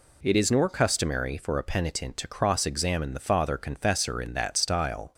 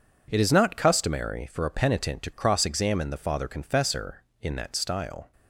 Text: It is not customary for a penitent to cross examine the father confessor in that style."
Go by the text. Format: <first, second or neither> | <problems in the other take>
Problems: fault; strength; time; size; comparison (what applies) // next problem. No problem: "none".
second | says "nor" for "not"; at 0.4 s